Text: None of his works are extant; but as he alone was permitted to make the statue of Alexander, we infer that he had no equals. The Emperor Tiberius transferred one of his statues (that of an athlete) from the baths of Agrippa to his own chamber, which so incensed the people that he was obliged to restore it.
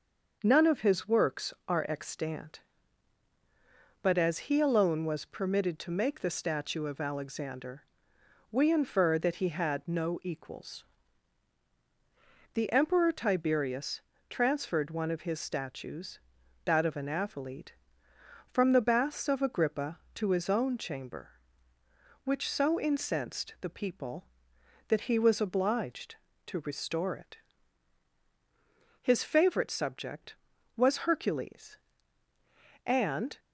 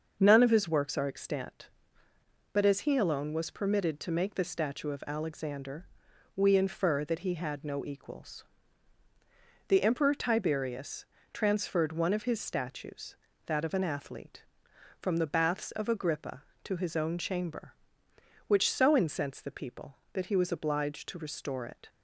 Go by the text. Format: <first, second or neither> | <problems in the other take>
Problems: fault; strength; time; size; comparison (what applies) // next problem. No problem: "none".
second | starts louder than the rest; until 1.4 s; 6 dB; also in the second // pauses between "Tiberius" and "transferred"; slight; at 13.9 s; 0.30 s long; slight in the second // goes on to say "His favorite subject was Hercules and"; strong; from 29.0 s on; 4.3 s long